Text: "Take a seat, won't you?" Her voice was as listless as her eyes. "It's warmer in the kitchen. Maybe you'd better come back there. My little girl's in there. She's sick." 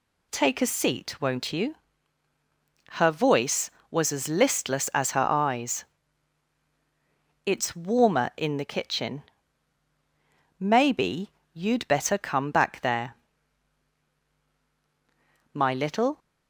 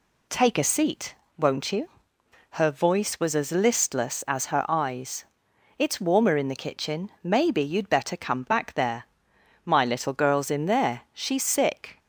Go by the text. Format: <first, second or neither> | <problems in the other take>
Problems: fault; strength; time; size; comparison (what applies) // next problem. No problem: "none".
second | pauses between "Maybe" and "you'd"; slight; at 11.3 s; 0.24 s long // stops before "girl's in there She's sick"; at 16.1 s